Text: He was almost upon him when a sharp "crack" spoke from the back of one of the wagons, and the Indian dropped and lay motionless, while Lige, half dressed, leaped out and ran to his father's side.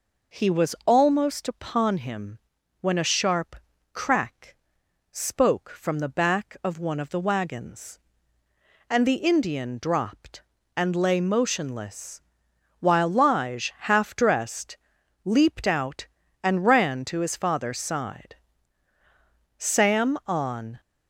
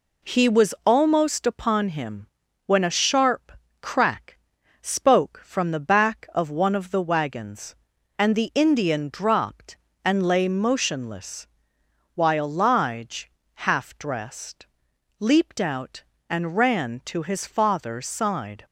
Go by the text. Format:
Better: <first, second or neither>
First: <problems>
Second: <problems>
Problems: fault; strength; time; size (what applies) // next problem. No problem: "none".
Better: second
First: pauses between "him" and "when"; at 2.3 s; 0.42 s long // pauses between "sharp" and "crack"; at 3.5 s; 0.38 s long // pauses between "crack" and "spoke"; noticeable; at 4.5 s; 0.56 s long // goes on to say "Sam on"; noticeable; from 19.5 s on; 1.2 s long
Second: pauses between "him" and "when"; at 2.2 s; 0.38 s long // pauses between "sharp" and "crack"; slight; at 3.5 s; 0.30 s long // pauses between "crack" and "spoke"; at 4.3 s; 0.44 s long